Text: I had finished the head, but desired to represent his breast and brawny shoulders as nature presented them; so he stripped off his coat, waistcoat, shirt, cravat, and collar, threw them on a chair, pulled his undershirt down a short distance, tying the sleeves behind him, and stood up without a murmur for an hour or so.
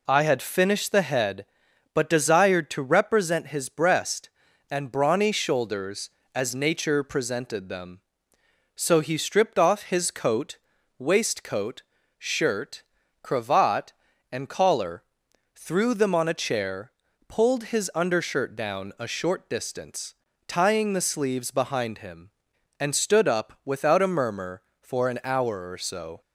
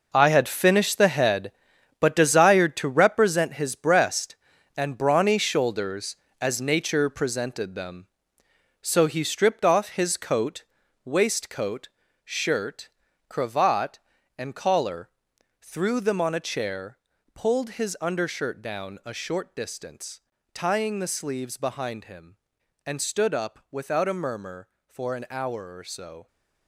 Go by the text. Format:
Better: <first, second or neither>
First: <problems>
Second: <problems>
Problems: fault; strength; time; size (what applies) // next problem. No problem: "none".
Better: first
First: none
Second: gets quieter; strong; throughout; 11.5 dB